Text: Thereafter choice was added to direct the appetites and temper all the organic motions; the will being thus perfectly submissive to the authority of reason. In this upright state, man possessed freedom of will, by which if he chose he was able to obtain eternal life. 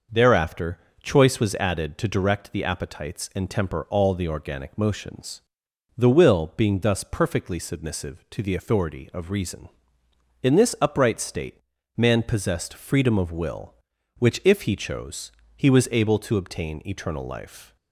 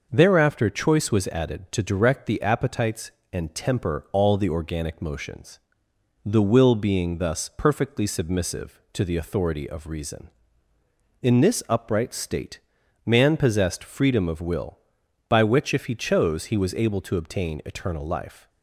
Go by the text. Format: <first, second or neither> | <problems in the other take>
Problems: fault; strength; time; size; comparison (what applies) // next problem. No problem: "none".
second | starts louder than the rest; noticeable; until 1.3 s; 6 dB // pauses between "Thereafter" and "choice"; slight; at 0.7 s; 0.24 s long // skips "by"; at 13.9 s // pauses between "chose" and "he"; slight; at 15.2 s; 0.26 s long